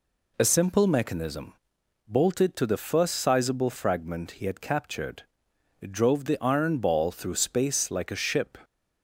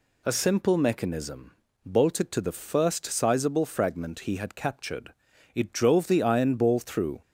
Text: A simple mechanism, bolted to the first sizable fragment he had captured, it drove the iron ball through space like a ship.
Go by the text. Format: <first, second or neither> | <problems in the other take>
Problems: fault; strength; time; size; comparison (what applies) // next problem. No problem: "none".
first | stops before "space like a ship"; at 7.2 s